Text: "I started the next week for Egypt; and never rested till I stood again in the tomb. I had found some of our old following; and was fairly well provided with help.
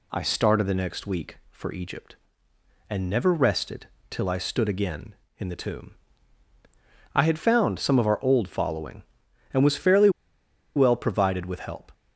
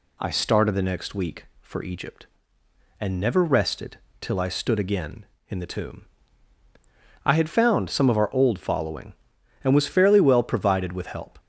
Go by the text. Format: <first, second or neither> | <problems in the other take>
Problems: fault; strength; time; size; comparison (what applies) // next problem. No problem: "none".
second | pauses between "rested" and "till"; slight; at 3.8 s; 0.22 s long; slight in the second // pauses between "fairly" and "well"; noticeable; at 10.0 s; 0.66 s long